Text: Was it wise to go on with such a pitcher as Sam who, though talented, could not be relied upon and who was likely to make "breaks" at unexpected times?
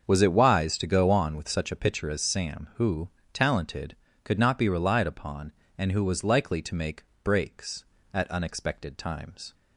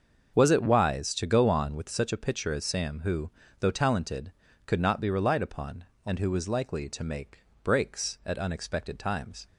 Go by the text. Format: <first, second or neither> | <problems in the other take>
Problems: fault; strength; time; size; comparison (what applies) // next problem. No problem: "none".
second | starts louder than the rest; until 1.0 s; 6.5 dB; also in the second // skips "though"; at 3.1 s // pauses between "make" and "breaks"; slight; at 7.0 s; 0.20 s long; slight in the second